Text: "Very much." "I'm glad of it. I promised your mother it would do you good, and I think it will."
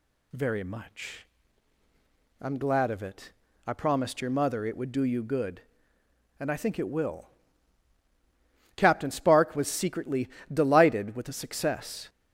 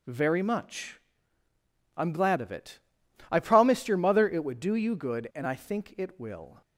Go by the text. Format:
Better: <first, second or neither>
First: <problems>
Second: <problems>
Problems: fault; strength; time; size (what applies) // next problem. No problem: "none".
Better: second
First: goes on to say "Captain Spark was secretly delighted with the success"; strong; from 8.7 s on; 3.3 s long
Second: none